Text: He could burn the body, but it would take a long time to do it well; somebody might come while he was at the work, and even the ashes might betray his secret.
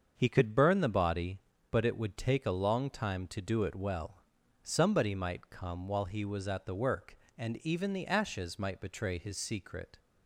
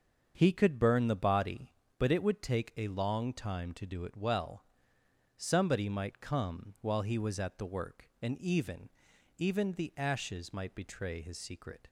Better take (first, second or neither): first